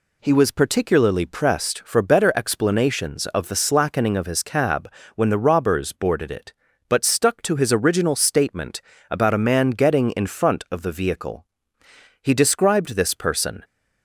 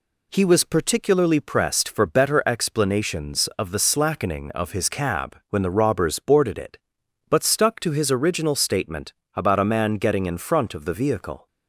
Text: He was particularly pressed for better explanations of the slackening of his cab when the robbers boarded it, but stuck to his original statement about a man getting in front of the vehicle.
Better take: second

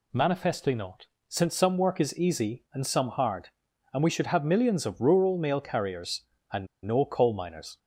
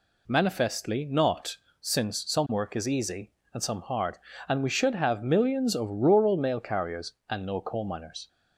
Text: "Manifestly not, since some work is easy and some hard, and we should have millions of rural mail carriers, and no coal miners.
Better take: second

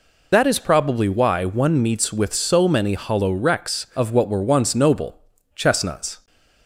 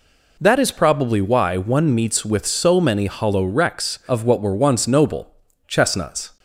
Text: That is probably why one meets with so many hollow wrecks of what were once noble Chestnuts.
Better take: second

